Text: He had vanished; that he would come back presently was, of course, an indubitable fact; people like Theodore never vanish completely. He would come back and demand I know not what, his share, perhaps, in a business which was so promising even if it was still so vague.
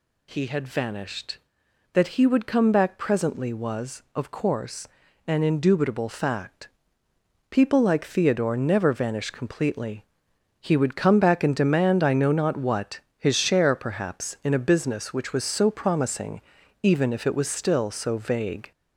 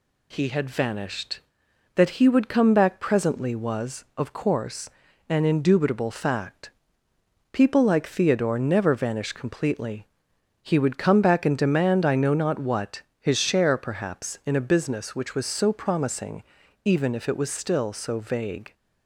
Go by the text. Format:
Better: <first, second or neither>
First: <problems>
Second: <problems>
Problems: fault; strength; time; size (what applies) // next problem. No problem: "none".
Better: second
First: gets louder; slight; throughout; 3 dB // pauses between "promising" and "even"; at 16.4 s; 0.42 s long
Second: pauses between "promising" and "even"; at 16.4 s; 0.42 s long